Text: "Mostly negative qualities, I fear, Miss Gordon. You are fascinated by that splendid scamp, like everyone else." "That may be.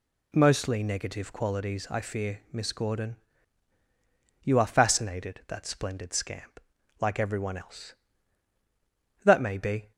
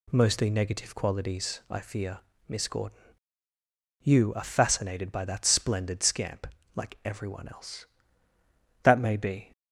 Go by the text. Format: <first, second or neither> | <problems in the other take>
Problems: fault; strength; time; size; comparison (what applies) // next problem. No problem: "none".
second | skips "by"; at 5.4 s